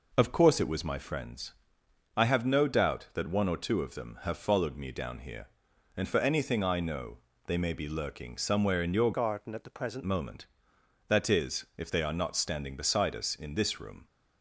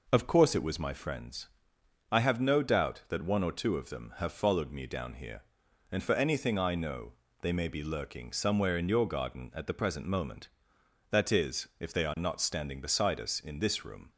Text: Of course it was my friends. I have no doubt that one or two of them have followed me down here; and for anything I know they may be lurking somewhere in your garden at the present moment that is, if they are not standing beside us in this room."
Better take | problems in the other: second | pauses between "know" and "they"; slight; at 7.1 s; 0.30 s long; slight in the second // changes voice from "garden" to "present"; from 9.1 to 10.0 s; 0.9 s long

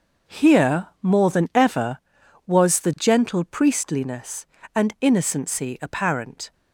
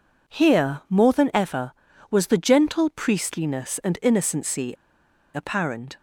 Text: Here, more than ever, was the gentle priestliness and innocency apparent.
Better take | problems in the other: first | pauses between "innocency" and "apparent"; noticeable; at 4.7 s; 0.59 s long

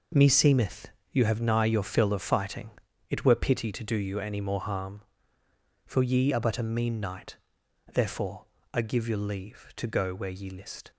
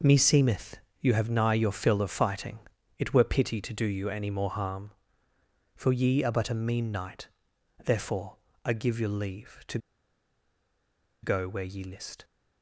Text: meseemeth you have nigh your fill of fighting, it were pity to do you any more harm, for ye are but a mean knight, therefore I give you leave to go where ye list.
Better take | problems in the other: first | pauses between "meseemeth" and "you"; slight; at 0.7 s; 0.22 s long; slight in the first // pauses between "therefore" and "I"; slight; at 8.3 s; 0.30 s long; slight in the first // pauses between "to" and "go"; strong; at 9.7 s; 1.4 s long

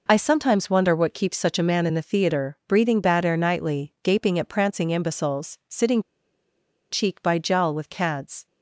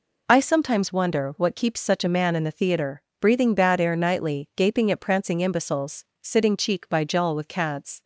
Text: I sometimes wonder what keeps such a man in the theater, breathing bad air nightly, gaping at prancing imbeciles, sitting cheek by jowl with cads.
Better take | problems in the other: second | pauses between "sitting" and "cheek"; noticeable; at 5.9 s; 0.91 s long

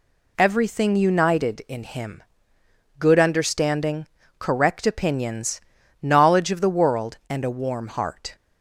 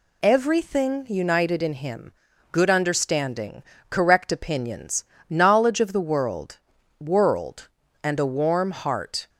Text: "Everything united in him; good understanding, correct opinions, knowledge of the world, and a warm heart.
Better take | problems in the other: first | says "world" twice; at 6.9 s

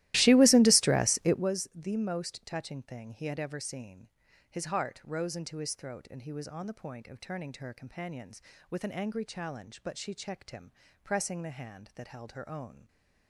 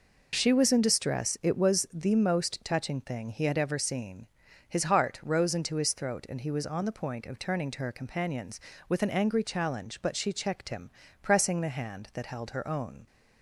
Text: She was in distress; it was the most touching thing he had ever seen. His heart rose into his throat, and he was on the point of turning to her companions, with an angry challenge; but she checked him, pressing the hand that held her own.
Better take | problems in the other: second | starts louder than the rest; strong; until 1.5 s; 16 dB

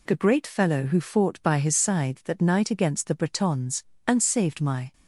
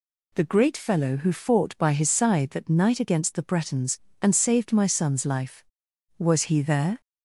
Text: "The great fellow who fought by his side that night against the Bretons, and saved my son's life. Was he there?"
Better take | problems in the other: second | stops before "son's life Was he there"; at 4.9 s

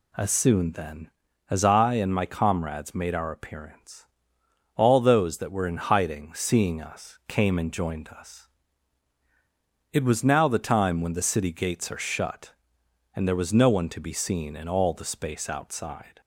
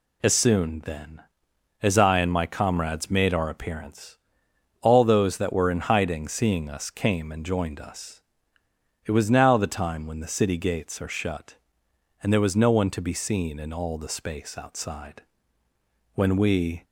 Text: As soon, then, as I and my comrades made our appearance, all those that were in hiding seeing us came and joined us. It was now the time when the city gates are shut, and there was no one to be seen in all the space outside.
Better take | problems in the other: first | goes on to say "When we"; noticeable; from 16.1 s on; 0.70 s long

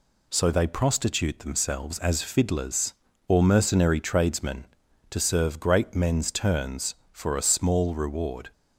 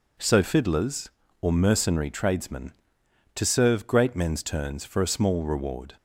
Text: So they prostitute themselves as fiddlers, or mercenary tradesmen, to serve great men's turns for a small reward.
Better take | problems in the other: first | skips "they prostitute themselves as"; at 0.4 s

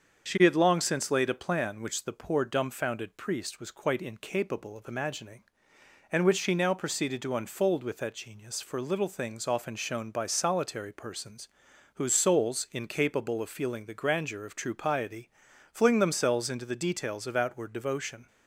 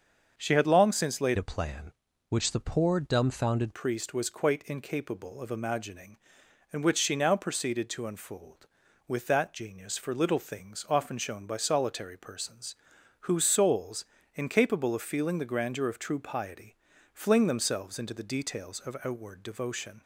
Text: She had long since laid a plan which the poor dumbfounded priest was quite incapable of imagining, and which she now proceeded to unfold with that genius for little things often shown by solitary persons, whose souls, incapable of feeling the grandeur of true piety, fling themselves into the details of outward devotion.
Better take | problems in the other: first | starts louder than the rest; until 1.3 s; 7 dB; also in the first // changes voice from "a" to "dumbfounded"; from 1.3 to 3.7 s; 2.4 s long

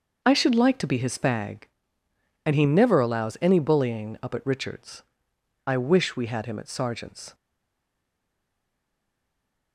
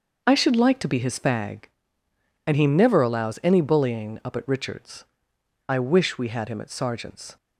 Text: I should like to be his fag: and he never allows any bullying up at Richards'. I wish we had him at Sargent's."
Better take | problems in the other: second | starts louder than the rest; noticeable; until 1.2 s; 6 dB; noticeable in the second // stays silent after the last word; from 7.3 s on; 2.4 s long

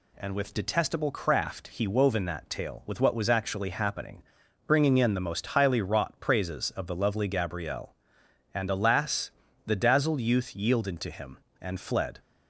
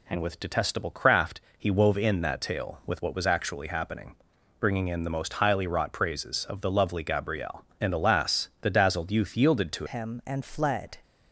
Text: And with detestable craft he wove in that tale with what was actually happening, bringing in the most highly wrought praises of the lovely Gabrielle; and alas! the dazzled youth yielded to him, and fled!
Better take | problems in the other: first | pauses between "craft" and "he"; slight; at 1.4 s; 0.18 s long // changes voice at "him"; from 9.8 s on; 1.1 s long

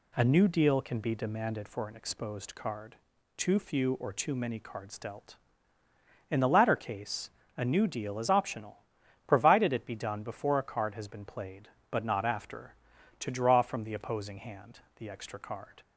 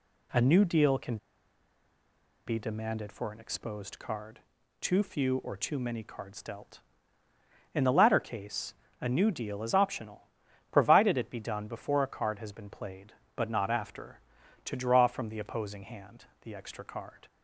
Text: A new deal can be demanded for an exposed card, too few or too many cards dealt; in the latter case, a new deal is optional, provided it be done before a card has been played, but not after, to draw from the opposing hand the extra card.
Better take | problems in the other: first | pauses between "can" and "be"; strong; at 1.1 s; 1.2 s long // pauses between "hand" and "the"; slight; at 16.2 s; 0.16 s long; slight in the first

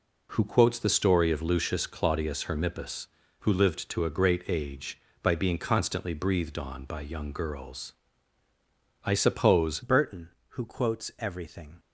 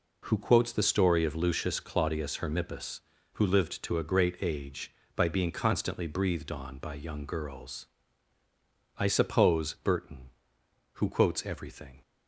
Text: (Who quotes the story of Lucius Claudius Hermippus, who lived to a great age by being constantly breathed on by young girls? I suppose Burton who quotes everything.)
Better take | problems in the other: second | changes voice at "Burton"; from 9.8 s on; 1.9 s long

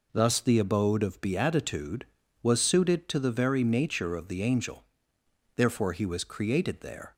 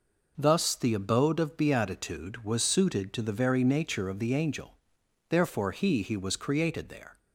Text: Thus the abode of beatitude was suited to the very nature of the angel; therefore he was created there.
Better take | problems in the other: first | says "he" twice; at 6.0 s

